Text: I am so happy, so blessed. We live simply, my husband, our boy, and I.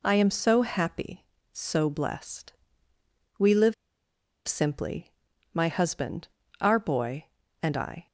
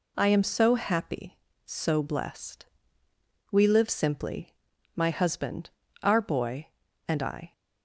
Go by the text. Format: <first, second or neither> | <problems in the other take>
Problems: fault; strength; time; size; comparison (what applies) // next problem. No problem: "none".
second | pauses between "live" and "simply"; noticeable; at 3.7 s; 0.72 s long